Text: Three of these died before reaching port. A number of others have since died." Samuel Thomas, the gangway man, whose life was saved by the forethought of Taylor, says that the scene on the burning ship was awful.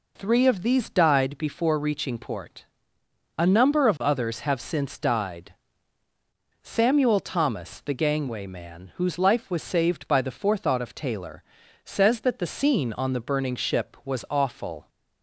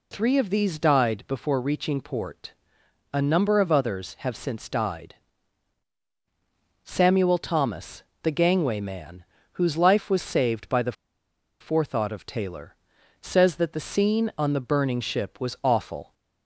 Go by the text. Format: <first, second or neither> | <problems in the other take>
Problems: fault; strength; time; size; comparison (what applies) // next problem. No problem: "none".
first | pauses between "the" and "forethought"; noticeable; at 10.9 s; 0.68 s long